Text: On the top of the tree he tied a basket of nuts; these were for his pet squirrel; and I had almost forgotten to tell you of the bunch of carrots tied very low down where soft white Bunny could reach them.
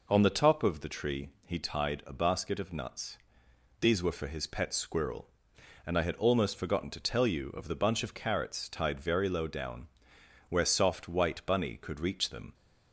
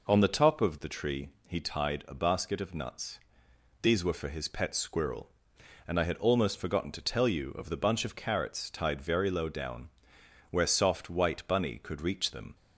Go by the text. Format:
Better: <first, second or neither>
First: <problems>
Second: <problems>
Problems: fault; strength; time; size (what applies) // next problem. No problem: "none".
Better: neither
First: pauses between "tree" and "he"; slight; at 1.2 s; 0.16 s long // pauses between "down" and "where"; noticeable; at 9.8 s; 0.60 s long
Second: pauses between "tree" and "he"; slight; at 1.2 s; 0.18 s long // pauses between "down" and "where"; noticeable; at 9.8 s; 0.60 s long